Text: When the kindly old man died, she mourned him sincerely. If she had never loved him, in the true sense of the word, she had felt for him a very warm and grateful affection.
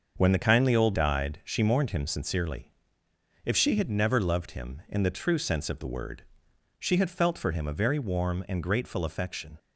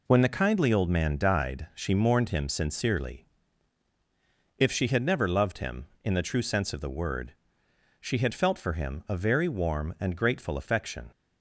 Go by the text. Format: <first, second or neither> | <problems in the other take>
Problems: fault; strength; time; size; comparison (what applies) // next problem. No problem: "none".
second | starts louder than the rest; until 1.1 s; 6 dB // skips "man"; at 0.9 s